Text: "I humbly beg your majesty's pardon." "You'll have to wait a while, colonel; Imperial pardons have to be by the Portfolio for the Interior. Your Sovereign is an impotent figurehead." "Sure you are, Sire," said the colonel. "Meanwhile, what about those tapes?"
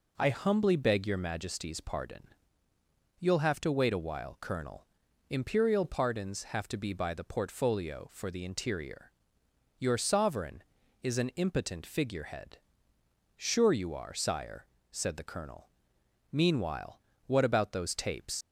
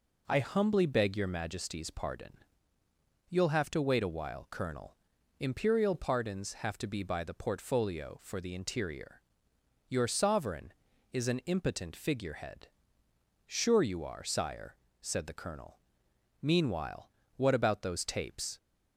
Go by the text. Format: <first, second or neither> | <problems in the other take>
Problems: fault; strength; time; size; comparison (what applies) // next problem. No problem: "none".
second | leaves "tapes" unfinished; at 18.4 s; 60 ms